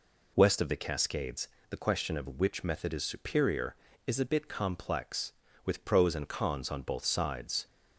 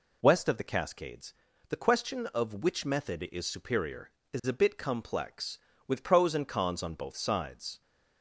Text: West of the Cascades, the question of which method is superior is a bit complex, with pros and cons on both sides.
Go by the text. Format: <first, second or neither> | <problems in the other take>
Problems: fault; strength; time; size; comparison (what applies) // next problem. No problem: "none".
neither | none